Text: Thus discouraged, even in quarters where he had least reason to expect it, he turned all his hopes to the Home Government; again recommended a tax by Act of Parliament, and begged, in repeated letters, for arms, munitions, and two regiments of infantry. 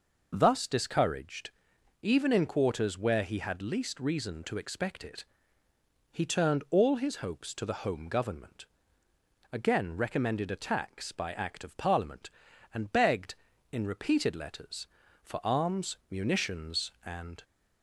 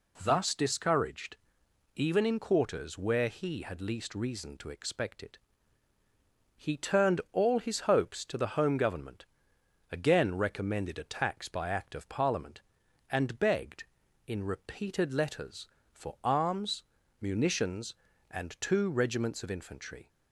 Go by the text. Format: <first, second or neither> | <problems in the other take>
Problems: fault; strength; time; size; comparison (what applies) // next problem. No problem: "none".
second | stops before "two regiments of infantry"; at 17.4 s